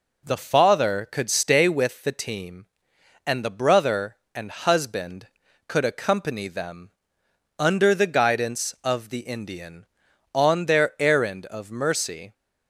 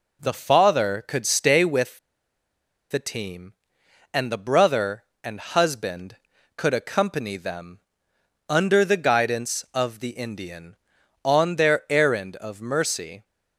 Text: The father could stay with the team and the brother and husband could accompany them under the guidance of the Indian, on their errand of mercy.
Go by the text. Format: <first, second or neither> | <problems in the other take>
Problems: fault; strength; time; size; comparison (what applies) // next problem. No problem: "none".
first | pauses between "with" and "the"; noticeable; at 1.9 s; 0.92 s long // pauses between "them" and "under"; noticeable; at 7.7 s; 0.68 s long; noticeable in the first